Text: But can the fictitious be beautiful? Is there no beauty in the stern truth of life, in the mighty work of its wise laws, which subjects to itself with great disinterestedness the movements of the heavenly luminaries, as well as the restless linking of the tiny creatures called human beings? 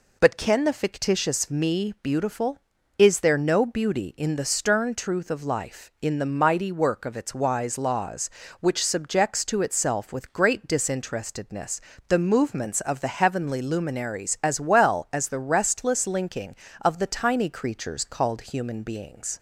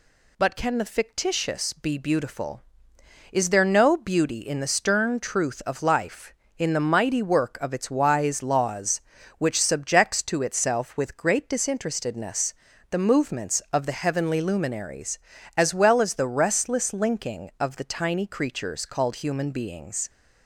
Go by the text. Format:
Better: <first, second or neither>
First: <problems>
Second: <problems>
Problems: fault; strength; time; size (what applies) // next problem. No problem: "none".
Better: second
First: says "me" for "be"; at 1.4 s // pauses between "disinterestedness" and "the"; slight; at 11.7 s; 0.28 s long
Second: pauses between "disinterestedness" and "the"; at 12.5 s; 0.38 s long